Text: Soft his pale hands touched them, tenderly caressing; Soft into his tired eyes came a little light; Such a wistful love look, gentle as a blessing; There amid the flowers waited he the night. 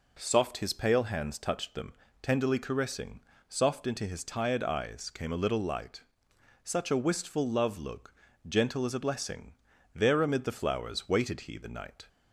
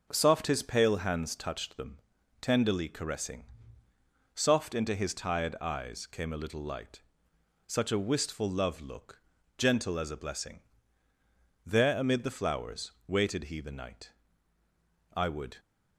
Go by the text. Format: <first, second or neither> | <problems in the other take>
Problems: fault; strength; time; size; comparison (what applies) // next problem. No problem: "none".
first | pauses between "flowers" and "waited"; slight; at 12.9 s; 0.16 s long // goes on to say "I would"; slight; from 15.1 s on; 0.46 s long